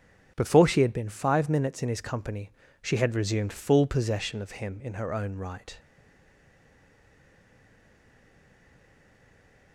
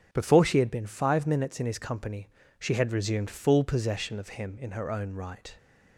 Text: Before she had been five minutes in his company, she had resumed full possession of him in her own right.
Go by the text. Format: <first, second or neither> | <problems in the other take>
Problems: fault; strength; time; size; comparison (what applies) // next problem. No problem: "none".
second | starts louder than the rest; strong; until 1.3 s; 7 dB; strong in the second // stays silent after the last word; strong; from 5.7 s on; 4.0 s long